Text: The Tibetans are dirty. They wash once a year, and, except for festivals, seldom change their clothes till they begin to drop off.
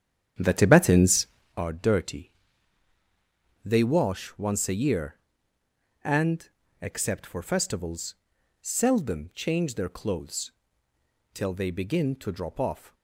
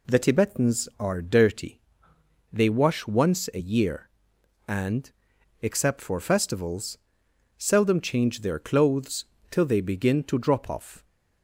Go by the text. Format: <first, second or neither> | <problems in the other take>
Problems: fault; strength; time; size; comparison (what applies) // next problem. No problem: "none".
second | starts louder than the rest; strong; until 1.6 s; 9 dB // pauses between "clothes" and "till"; noticeable; at 10.5 s; 0.82 s long; slight in the second